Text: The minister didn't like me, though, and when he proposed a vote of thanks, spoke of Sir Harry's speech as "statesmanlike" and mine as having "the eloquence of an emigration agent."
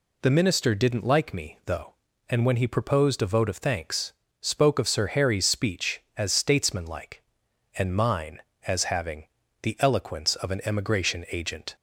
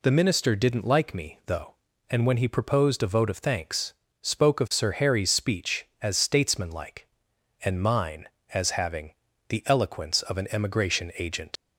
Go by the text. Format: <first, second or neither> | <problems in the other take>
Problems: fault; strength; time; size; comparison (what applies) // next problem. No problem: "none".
first | pauses between "having" and "the"; slight; at 9.1 s; 0.36 s long; slight in the first // leaves "agent" unfinished; at 11.5 s; 65 ms